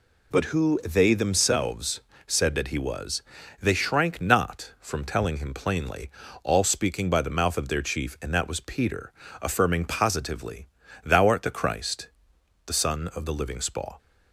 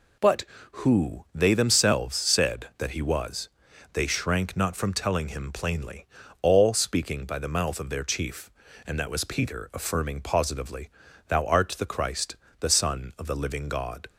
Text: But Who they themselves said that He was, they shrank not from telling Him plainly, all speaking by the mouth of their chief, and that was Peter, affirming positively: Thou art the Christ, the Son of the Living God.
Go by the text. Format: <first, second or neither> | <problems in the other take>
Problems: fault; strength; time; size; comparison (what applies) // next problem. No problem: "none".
second | pauses between "themselves" and "said"; slight; at 1.9 s; 0.26 s long // says "Spaw" for "God"; at 13.5 s